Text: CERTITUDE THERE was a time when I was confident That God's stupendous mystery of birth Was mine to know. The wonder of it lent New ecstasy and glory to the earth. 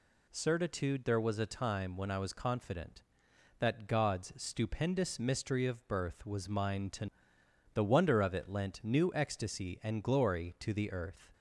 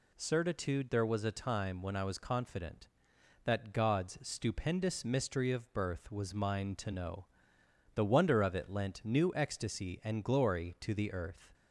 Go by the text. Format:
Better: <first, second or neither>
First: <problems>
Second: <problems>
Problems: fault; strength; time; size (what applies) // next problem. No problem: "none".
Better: second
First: skips "know"; at 7.3 s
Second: none